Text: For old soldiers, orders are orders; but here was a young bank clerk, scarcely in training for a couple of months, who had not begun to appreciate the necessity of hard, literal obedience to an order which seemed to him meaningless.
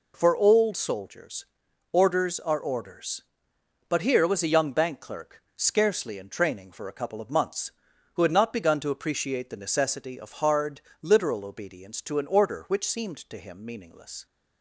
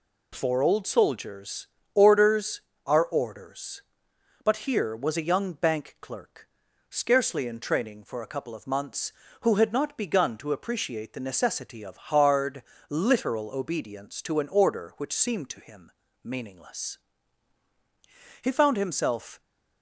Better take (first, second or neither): first